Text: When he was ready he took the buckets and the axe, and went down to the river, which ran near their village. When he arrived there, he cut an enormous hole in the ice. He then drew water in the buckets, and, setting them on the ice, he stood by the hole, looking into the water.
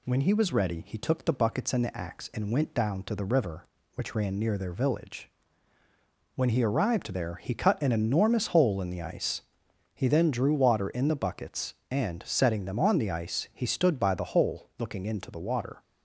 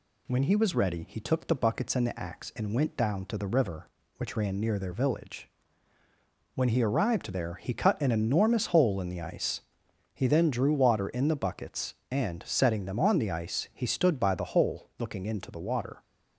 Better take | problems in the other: neither | none

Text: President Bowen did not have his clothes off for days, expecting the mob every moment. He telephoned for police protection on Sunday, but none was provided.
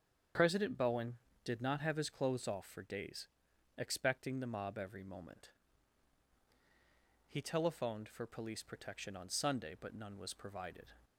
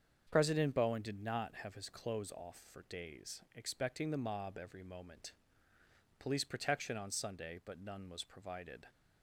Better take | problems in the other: first | starts louder than the rest; strong; until 1.3 s; 7 dB; strong in the first // skips "He telephoned for"; at 5.7 s

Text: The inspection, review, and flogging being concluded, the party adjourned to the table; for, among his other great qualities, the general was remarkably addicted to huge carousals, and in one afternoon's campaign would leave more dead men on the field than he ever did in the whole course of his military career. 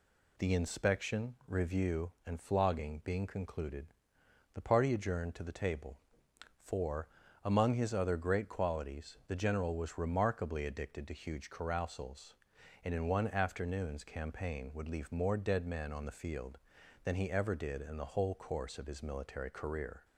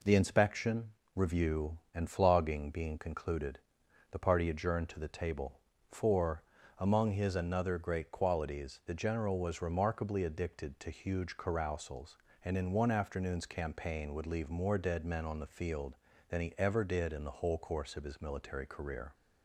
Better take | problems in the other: first | says "another" for "other"; at 7.3 s

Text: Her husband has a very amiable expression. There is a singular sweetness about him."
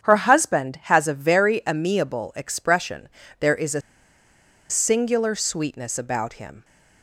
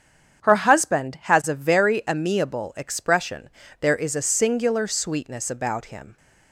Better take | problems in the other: second | starts louder than the rest; strong; until 1.0 s; 7.5 dB; strong in the second // pauses between "a" and "singular"; noticeable; at 3.8 s; 0.89 s long

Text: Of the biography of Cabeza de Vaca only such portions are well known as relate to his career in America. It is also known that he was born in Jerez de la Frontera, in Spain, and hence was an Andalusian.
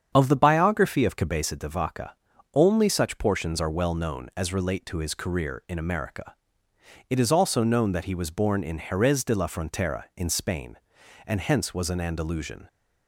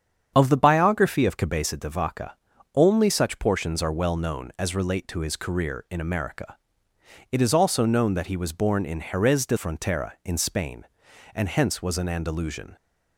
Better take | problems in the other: first | starts louder than the rest; strong; until 1.3 s; 8 dB; strong in the first // pauses between "Vaca" and "only"; at 2.3 s; 0.40 s long; also in the first // skips "la"; at 9.5 s

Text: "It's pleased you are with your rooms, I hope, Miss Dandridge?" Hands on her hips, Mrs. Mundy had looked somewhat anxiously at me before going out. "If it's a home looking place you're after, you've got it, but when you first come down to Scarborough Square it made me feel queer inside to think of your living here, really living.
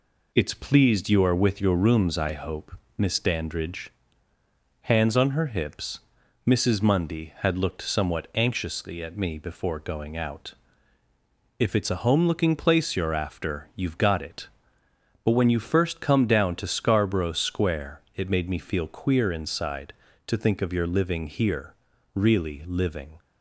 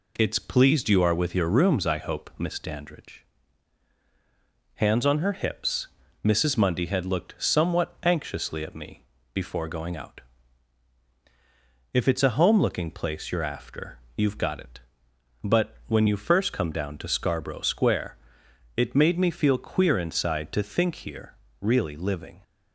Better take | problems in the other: first | pauses between "me" and "before"; slight; at 9.0 s; 0.30 s long // pauses between "Square" and "it"; noticeable; at 18.1 s; 0.62 s long // skips "of your living"; at 20.9 s

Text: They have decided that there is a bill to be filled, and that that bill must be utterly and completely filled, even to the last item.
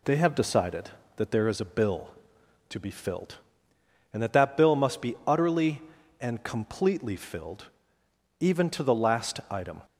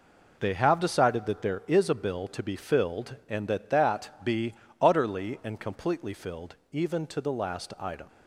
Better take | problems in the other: first | skips "bill must"; at 4.2 s // pauses between "be" and "utterly"; slight; at 4.5 s; 0.28 s long

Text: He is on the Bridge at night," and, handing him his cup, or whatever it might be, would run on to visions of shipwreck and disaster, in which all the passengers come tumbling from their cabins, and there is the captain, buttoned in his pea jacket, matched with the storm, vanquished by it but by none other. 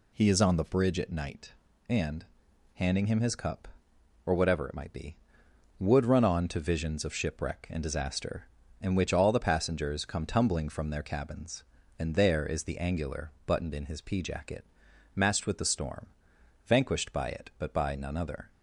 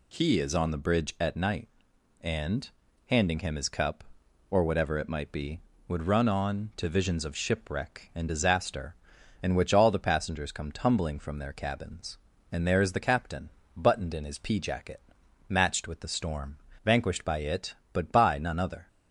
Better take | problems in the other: second | says "angular" for "captain"; at 12.7 s

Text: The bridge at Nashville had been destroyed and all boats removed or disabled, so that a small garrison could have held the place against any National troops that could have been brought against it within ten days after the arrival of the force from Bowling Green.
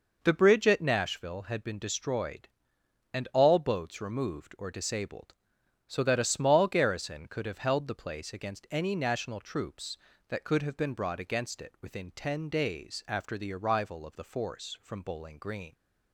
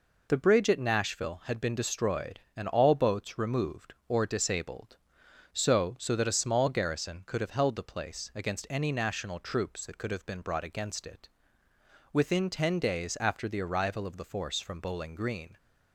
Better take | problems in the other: first | says "so" twice; at 5.9 s // pauses between "it" and "within"; noticeable; at 11.2 s; 0.86 s long

